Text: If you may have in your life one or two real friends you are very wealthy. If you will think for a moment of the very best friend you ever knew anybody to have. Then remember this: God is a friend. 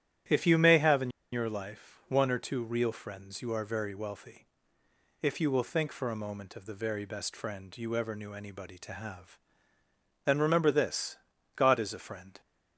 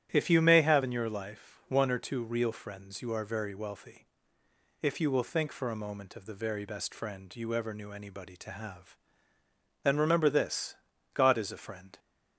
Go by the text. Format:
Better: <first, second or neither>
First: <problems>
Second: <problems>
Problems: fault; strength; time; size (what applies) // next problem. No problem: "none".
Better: second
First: starts louder than the rest; strong; until 1.5 s; 11.5 dB // pauses between "in" and "your"; slight; at 1.0 s; 0.23 s long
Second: starts louder than the rest; strong; until 1.1 s; 11.5 dB